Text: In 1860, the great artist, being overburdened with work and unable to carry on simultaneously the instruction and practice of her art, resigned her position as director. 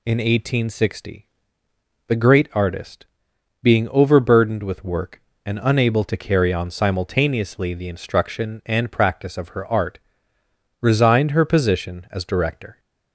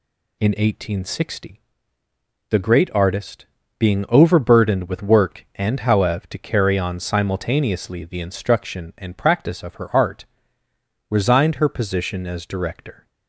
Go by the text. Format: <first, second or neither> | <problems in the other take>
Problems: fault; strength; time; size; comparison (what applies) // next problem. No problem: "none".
first | says "howev" for "unable"; at 5.8 s